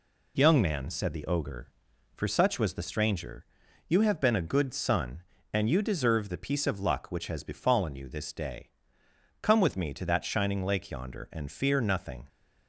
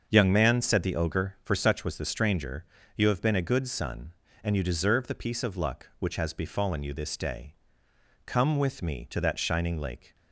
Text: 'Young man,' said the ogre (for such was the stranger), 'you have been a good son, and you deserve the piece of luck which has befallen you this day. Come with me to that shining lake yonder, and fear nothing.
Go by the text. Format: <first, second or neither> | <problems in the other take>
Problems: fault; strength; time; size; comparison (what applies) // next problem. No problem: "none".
first | starts louder than the rest; until 1.0 s; 6.5 dB // stops before "yonder and fear nothing"; at 10.1 s